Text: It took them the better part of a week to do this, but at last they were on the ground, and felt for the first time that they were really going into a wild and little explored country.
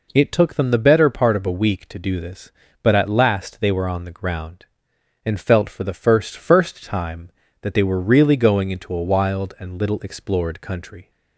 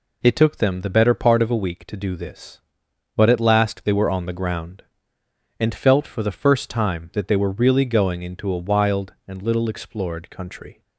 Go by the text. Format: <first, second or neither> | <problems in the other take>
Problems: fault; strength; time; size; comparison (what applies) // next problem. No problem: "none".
second | says "first" twice; at 6.3 s